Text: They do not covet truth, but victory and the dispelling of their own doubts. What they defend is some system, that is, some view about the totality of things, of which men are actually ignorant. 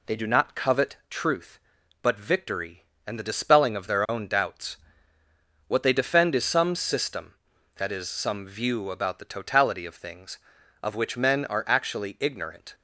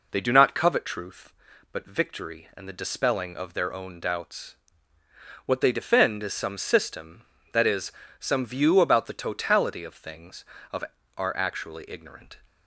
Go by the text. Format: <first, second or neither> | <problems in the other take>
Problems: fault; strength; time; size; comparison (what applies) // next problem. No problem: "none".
first | skips "which men"; at 11.0 s